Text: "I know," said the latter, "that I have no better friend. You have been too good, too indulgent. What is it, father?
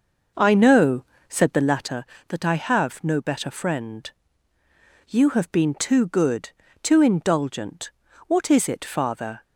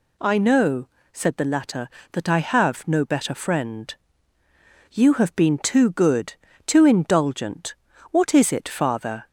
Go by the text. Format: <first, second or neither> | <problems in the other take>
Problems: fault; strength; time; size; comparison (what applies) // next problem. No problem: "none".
second | starts louder than the rest; noticeable; until 2.1 s; 6 dB